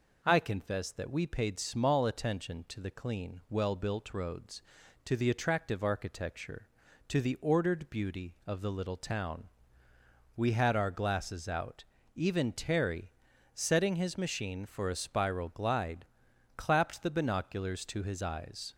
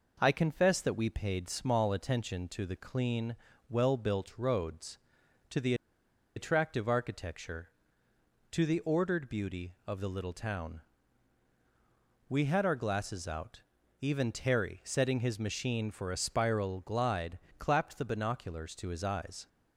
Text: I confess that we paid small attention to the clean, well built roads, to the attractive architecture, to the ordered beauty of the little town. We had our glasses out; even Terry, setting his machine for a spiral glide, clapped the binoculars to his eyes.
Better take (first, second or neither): first